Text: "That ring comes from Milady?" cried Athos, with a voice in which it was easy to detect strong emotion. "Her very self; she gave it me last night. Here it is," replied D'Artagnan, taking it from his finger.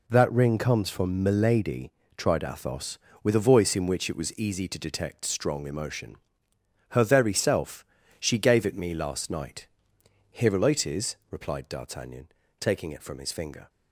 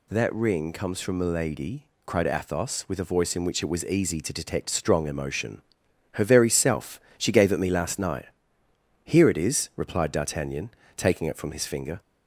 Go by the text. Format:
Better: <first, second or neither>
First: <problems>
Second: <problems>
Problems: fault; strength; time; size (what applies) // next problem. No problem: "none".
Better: second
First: says "tried" for "cried"; at 2.1 s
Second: none